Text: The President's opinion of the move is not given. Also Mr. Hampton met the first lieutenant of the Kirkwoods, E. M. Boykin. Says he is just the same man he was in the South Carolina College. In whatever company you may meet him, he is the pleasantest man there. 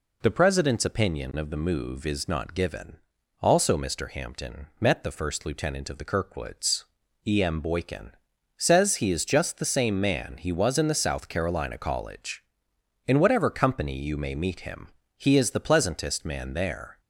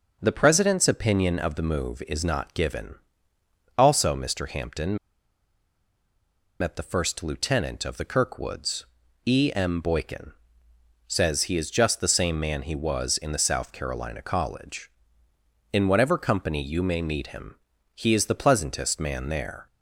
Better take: first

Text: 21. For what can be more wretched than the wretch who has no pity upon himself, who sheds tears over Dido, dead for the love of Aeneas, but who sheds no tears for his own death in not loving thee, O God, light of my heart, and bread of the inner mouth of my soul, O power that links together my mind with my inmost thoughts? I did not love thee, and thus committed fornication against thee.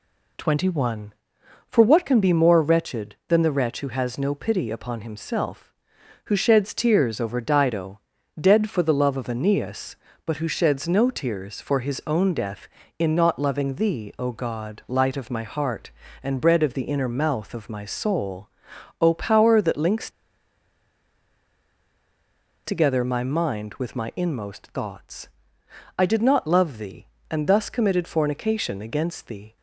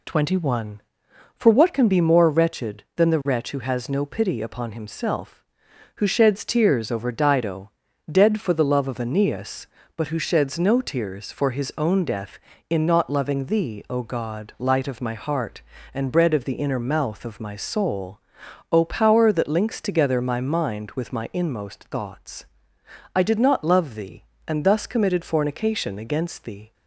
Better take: second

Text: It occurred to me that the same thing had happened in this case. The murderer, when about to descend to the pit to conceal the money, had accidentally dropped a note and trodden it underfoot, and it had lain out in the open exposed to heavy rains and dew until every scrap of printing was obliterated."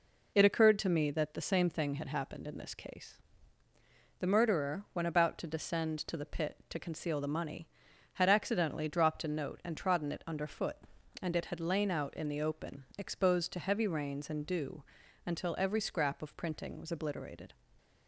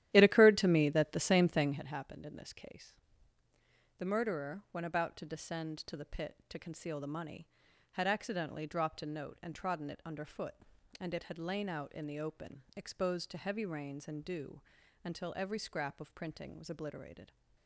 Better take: first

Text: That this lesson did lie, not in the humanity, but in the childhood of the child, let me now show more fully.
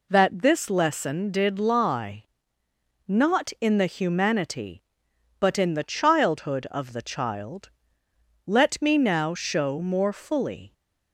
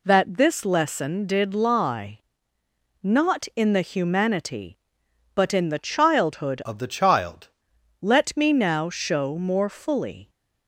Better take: first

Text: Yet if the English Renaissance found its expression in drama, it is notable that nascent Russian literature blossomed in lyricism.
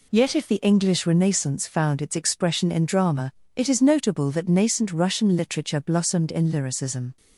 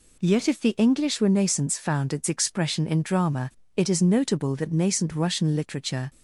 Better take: first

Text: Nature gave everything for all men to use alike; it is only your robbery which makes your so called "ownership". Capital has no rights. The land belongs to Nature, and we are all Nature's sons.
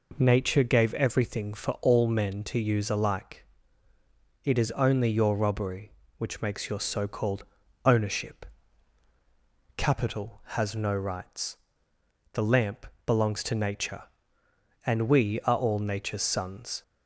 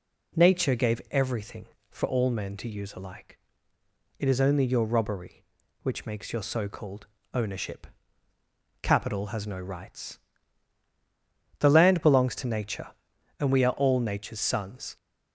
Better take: second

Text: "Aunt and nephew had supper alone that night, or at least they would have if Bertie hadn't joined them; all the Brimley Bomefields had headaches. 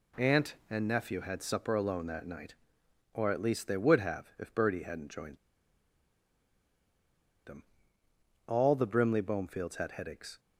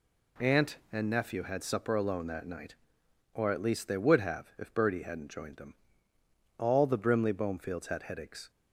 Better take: second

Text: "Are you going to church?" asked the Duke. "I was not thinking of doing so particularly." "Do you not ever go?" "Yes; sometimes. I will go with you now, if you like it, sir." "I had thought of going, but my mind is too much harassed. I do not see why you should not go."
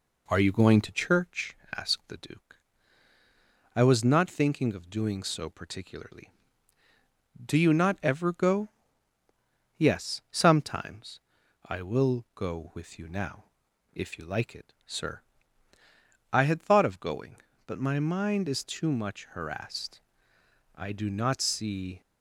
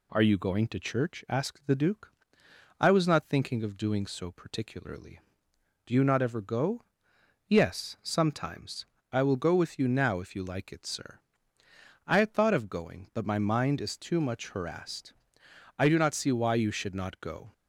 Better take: second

